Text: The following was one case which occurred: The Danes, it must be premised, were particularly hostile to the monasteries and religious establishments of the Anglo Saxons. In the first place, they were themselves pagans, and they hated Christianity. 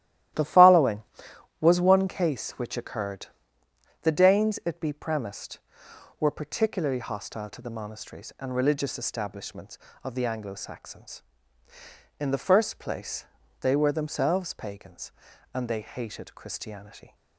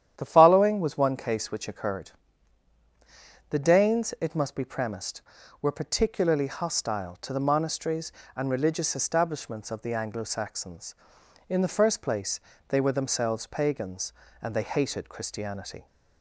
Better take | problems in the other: second | starts louder than the rest; strong; until 1.9 s; 14 dB; strong in the second // skips "must"; at 4.8 s

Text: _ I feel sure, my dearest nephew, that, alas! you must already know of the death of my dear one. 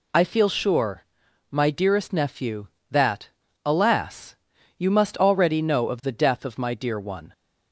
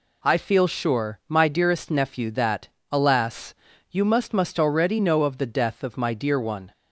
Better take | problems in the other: first | says "must" twice; at 4.3 s

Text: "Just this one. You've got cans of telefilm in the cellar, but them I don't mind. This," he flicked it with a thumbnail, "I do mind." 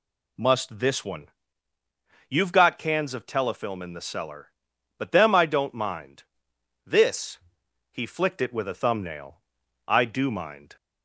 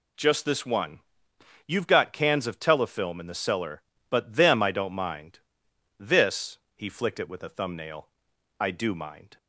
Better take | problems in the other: second | says "Must" for "Just"; at 0.3 s

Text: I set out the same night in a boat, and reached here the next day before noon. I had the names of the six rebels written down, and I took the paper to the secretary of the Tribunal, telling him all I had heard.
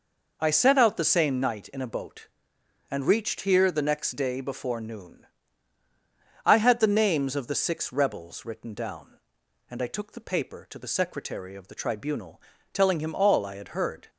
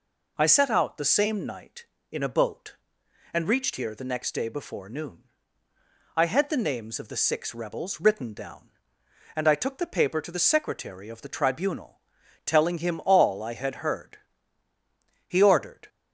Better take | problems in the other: first | goes on to say "He ordered"; from 15.2 s on; 0.60 s long

